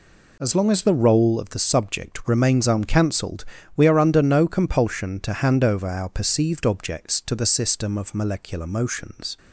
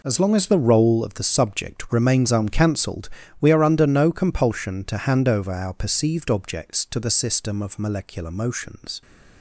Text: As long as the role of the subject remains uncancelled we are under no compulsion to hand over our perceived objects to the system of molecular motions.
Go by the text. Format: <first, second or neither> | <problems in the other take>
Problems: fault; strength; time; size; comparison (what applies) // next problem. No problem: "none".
first | gets quieter; strong; throughout; 12 dB // pauses between "uncancelled" and "we"; slight; at 3.0 s; 0.32 s long; slight in the first